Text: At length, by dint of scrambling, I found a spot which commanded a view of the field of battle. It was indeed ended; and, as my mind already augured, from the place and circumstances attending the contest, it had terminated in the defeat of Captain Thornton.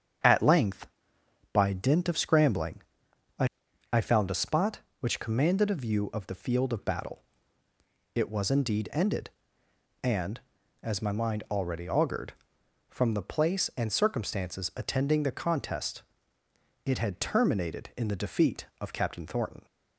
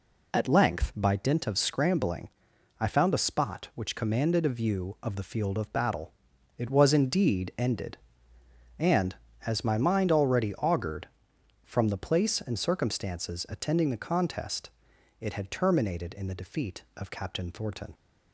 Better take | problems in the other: second | starts louder than the rest; strong; until 1.9 s; 8 dB // says "I" twice; at 3.9 s

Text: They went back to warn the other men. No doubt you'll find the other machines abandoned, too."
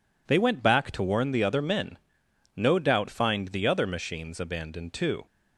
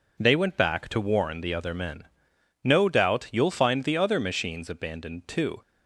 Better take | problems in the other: second | skips "you'll"; at 3.0 s

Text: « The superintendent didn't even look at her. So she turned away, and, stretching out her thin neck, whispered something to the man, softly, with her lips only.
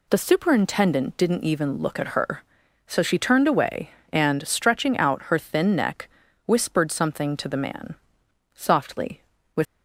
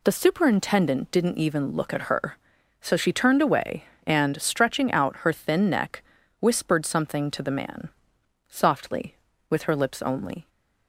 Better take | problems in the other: second | stops before "her lips only"; at 9.6 s

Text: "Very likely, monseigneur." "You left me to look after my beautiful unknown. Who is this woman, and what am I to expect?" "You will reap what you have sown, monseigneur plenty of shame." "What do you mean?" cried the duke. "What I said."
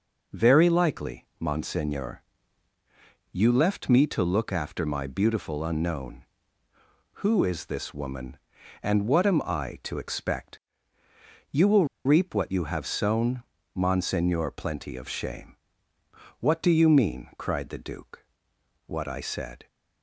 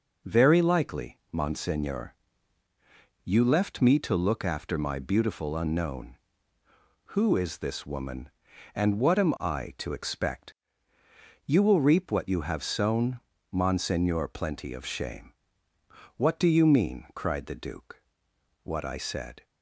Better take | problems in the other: second | pauses between "will" and "reap"; slight; at 11.8 s; 0.20 s long

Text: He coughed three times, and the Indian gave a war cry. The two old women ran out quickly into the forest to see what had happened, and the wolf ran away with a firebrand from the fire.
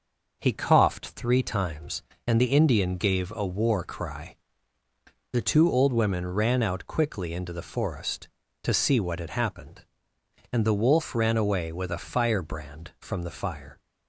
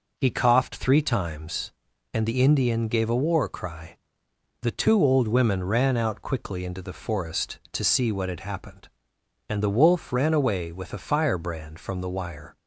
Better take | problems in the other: first | says "wire" for "fire"; at 12.0 s

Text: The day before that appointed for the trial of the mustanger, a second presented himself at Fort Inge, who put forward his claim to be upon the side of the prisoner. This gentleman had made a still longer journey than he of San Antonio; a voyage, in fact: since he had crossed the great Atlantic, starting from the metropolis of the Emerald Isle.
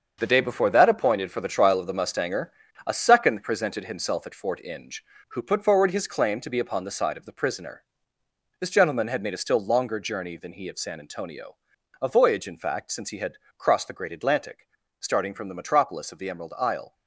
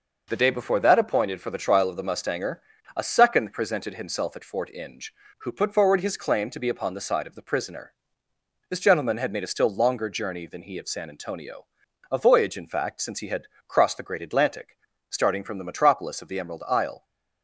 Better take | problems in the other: second | gets quieter; strong; throughout; 8.5 dB // pauses between "had" and "crossed"; slight; at 13.3 s; 0.20 s long; slight in the second

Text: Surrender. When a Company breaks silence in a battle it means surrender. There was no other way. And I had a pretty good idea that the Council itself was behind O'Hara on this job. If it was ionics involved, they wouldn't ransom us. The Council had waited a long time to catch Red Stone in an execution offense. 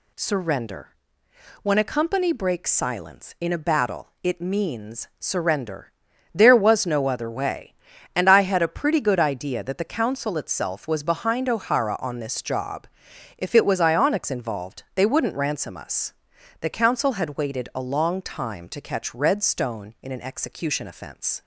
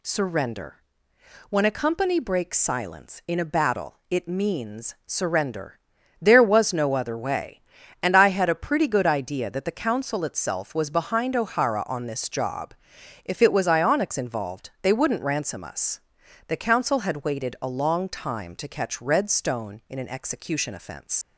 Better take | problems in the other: first | leaves "offense" unfinished; at 21.2 s; 70 ms

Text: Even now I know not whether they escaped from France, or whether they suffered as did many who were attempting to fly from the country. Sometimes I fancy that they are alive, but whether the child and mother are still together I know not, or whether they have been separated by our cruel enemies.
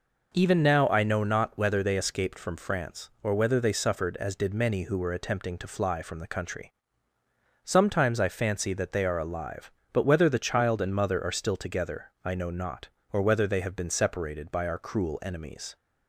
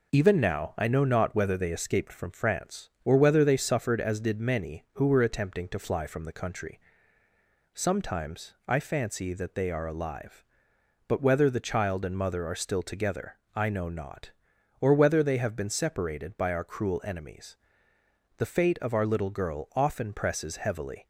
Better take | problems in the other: first | pauses between "together" and "I"; slight; at 13.3 s; 0.16 s long // goes on to say "The fate of our little girl often presses heavily"; strong; from 18.3 s on; 2.7 s long

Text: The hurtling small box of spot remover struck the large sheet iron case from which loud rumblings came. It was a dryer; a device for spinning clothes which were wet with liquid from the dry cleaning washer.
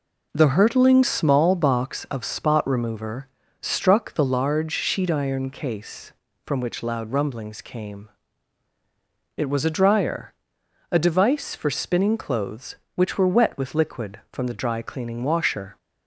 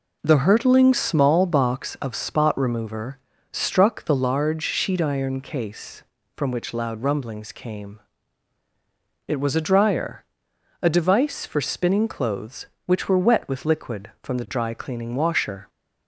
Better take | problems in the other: neither | pauses between "remover" and "struck"; slight; the same in both

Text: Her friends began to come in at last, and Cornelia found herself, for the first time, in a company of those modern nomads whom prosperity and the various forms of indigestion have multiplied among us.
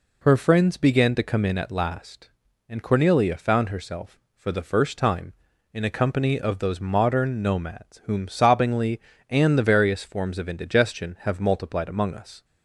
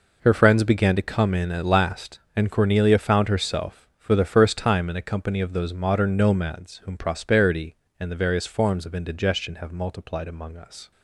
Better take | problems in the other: second | says "sobbingly" for "prosperity"; at 8.2 s

